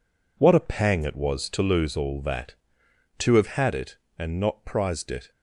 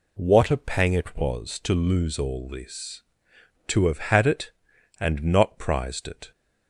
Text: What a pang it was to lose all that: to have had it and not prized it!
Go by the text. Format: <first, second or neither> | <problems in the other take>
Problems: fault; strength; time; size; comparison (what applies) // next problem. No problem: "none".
first | says "this" for "that"; at 2.4 s